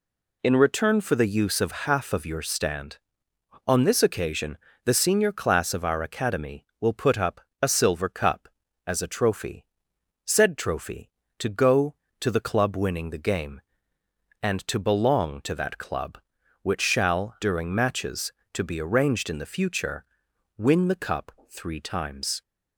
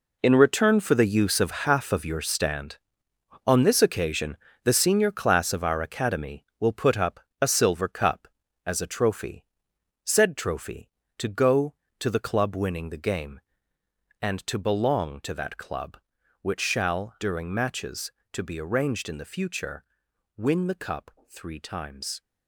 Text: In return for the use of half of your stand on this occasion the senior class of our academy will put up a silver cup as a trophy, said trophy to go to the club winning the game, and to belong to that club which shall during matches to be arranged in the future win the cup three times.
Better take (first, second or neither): first